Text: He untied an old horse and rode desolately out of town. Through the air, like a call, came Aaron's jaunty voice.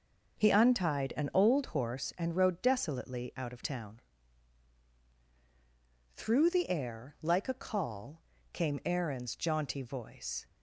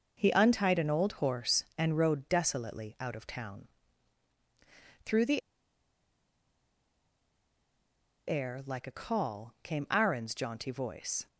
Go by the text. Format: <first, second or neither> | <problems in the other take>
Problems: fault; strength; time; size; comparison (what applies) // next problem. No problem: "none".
first | pauses between "the" and "air"; strong; at 5.4 s; 2.8 s long